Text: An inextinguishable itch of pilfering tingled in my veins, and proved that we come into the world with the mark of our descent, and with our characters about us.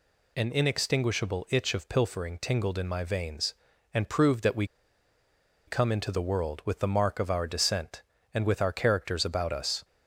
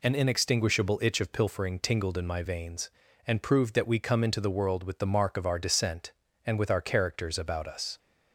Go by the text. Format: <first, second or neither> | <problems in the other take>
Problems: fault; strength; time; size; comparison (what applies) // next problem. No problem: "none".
second | pauses between "we" and "come"; at 4.6 s; 1.0 s long